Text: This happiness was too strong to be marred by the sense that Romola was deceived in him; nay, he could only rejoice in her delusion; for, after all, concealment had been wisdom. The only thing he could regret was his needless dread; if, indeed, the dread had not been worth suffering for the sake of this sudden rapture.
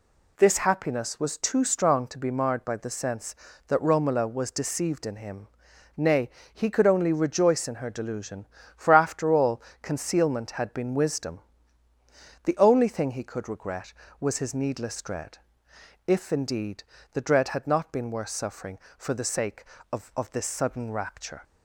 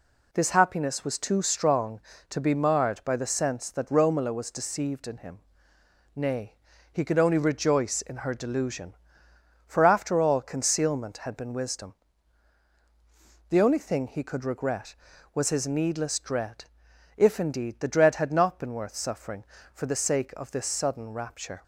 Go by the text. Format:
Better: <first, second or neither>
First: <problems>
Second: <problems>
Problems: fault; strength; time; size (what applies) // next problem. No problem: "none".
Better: second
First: says "of" twice; at 20.1 s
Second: none